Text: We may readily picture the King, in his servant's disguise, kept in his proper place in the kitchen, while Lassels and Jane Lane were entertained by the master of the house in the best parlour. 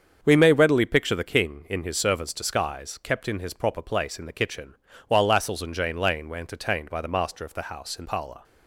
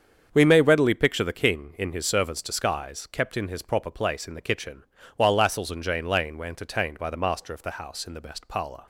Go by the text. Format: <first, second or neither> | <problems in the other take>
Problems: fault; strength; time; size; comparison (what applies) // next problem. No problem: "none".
second | starts louder than the rest; until 1.2 s; 7 dB; strong in the second // skips "the best"; at 8.0 s